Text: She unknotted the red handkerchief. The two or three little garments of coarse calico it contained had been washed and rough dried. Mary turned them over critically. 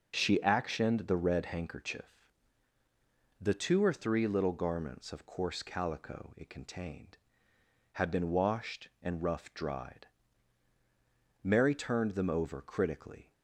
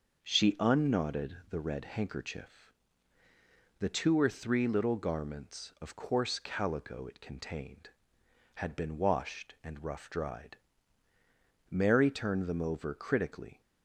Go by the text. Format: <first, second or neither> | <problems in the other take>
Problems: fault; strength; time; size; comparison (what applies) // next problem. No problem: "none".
second | says "actioned" for "unknotted"; at 0.3 s